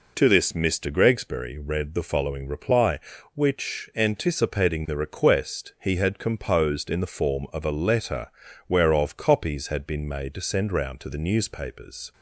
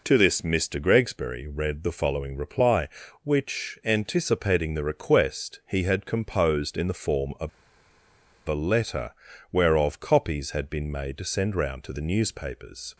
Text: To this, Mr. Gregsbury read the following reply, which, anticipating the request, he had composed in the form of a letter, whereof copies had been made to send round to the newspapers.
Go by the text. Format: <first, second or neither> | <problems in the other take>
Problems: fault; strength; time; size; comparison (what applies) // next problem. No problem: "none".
first | pauses between "of" and "a"; noticeable; at 7.4 s; 0.97 s long